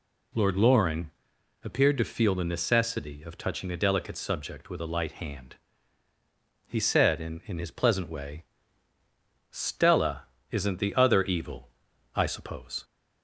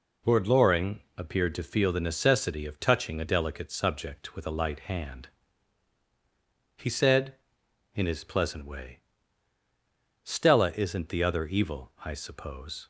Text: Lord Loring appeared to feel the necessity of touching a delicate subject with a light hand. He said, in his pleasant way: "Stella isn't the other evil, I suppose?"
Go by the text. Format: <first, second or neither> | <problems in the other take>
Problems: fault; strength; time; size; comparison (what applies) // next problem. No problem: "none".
second | pauses between "Loring" and "appeared"; noticeable; at 1.0 s; 0.54 s long; slight in the second // says "in" twice; at 7.4 s // pauses between "Stella" and "isn't"; slight; at 10.2 s; 0.26 s long